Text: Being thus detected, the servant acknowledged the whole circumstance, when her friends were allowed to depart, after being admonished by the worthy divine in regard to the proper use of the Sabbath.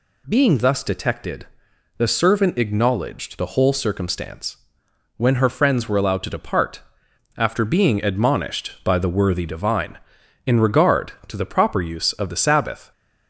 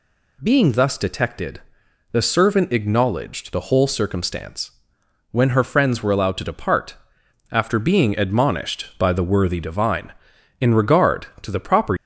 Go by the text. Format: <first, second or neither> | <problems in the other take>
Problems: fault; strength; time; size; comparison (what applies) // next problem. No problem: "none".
first | stops before "use of the Sabbath"; at 11.9 s